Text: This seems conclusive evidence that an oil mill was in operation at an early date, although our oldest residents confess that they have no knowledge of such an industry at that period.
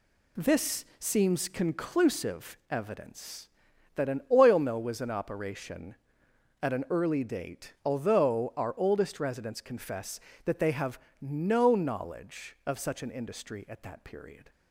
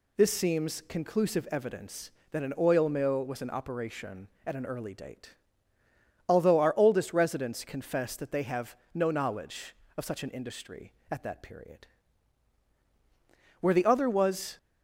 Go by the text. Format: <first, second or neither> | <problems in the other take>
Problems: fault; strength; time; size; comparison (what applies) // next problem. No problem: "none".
first | pauses between "have" and "no"; slight; at 8.7 s; 0.18 s long; slight in the first // goes on to say "Where the other was"; noticeable; from 13.5 s on; 0.98 s long